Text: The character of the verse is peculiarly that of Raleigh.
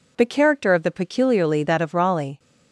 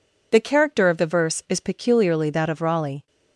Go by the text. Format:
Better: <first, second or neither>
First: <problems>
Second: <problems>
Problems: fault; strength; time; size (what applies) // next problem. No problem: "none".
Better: second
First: skips "verse is"; at 0.9 s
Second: none